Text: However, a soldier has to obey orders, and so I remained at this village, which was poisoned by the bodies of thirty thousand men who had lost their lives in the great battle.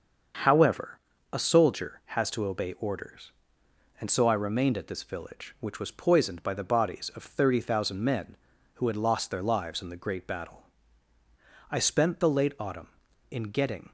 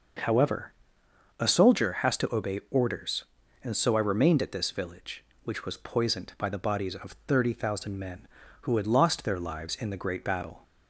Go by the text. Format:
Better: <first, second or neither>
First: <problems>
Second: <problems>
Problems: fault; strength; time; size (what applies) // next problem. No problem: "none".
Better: second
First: starts louder than the rest; until 1.7 s; 6.5 dB // goes on to say "I spent the late autumn in getting"; strong; from 11.7 s on; 2.2 s long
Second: none